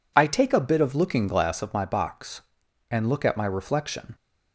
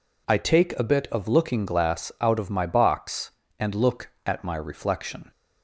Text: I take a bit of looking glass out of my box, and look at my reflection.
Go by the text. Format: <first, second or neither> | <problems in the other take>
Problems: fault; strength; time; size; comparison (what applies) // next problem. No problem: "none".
second | skips "out"; at 1.6 s